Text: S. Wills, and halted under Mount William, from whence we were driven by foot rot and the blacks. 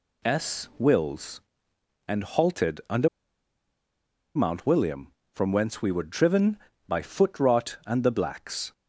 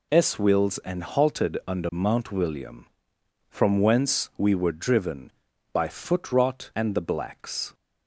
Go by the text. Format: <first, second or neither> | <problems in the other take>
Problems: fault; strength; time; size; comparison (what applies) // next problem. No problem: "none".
second | pauses between "under" and "Mount"; strong; at 3.0 s; 1.2 s long